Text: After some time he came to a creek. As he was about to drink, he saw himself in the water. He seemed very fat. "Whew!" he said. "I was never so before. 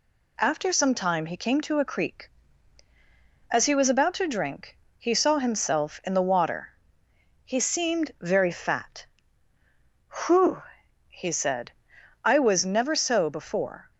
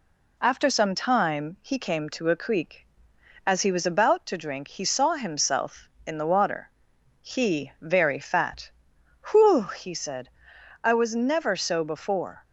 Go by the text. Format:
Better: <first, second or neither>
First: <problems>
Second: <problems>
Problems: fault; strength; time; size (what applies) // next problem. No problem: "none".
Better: first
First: none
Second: skips "seemed"; at 7.7 s